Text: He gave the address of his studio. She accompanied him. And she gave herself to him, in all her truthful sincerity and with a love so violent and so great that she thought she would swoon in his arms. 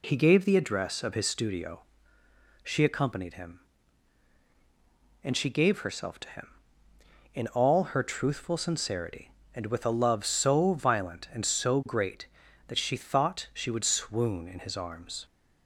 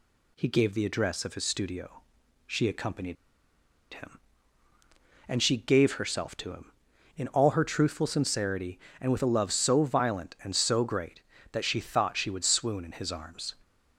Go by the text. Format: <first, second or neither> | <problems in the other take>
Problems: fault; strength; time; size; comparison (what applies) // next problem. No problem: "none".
first | pauses between "accompanied" and "him"; noticeable; at 3.1 s; 0.78 s long